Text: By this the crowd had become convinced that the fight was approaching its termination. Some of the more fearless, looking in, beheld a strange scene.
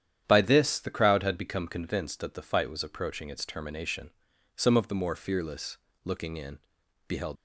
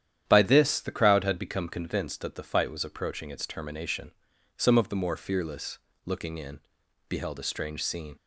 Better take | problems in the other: second | starts louder than the rest; strong; until 1.2 s; 10 dB; strong in the second // stops before "a strange scene"; at 7.3 s

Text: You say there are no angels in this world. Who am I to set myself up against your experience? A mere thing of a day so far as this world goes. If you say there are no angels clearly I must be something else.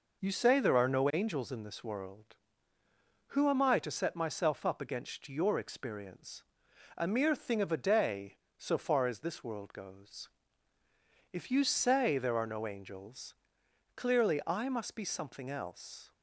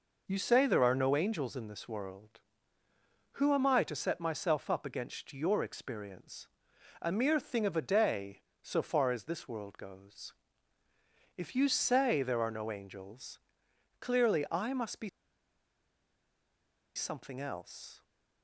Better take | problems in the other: first | pauses between "angels" and "clearly"; noticeable; at 13.3 s; 0.60 s long; noticeable in the first // pauses between "be" and "something"; strong; at 15.0 s; 1.8 s long

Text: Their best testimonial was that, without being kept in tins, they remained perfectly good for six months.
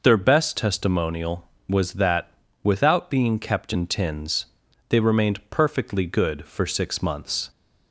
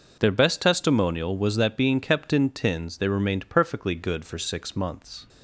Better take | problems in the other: first | skips "without"; at 1.7 s

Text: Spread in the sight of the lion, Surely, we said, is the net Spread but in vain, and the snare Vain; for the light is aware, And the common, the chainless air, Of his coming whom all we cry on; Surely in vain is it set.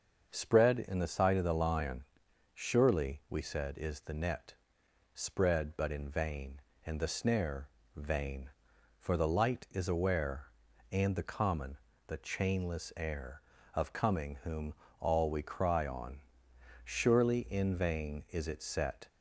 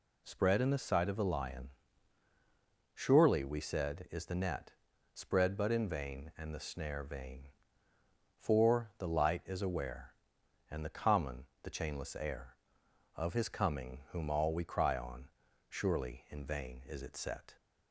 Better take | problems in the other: second | starts louder than the rest; until 1.3 s; 6.5 dB // pauses between "net" and "Spread"; noticeable; at 4.5 s; 0.62 s long; also in the second // pauses between "snare" and "Vain"; slight; at 7.6 s; 0.28 s long // skips "his"; at 13.9 s // pauses between "whom" and "all"; slight; at 14.7 s; 0.24 s long

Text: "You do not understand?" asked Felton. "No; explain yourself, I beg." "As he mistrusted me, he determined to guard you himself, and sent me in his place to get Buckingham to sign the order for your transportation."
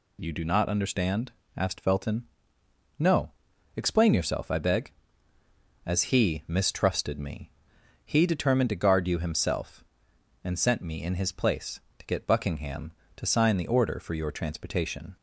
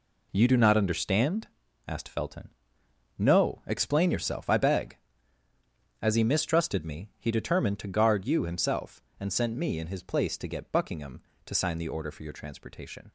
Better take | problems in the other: first | gets quieter; strong; throughout; 9 dB

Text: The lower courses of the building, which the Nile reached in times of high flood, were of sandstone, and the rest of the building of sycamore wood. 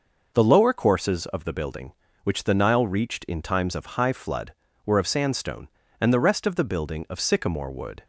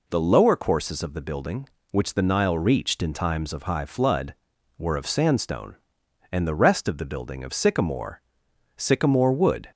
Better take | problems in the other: first | says "sycamore" twice; at 8.7 s

